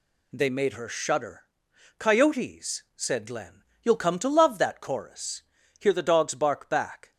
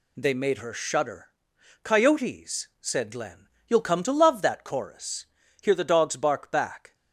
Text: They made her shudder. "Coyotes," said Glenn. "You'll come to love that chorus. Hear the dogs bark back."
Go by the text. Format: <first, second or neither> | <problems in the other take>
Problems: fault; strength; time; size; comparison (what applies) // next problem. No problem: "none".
neither | none